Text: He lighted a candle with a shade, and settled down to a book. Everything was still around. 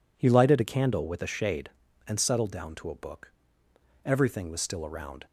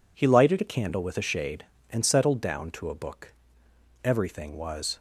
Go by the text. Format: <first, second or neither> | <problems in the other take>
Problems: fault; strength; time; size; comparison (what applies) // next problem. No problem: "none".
first | stops before "still around"; at 4.9 s